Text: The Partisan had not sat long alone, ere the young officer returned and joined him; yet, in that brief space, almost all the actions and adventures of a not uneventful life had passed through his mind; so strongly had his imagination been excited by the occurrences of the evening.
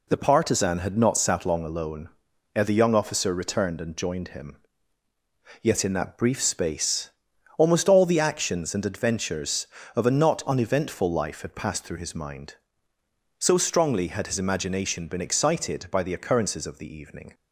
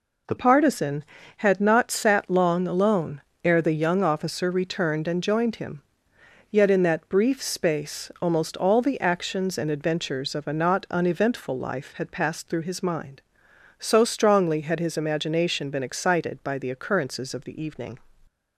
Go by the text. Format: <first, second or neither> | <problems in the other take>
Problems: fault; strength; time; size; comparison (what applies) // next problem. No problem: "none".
first | changes voice at "Partisan"; from 0.3 s on; 17.6 s long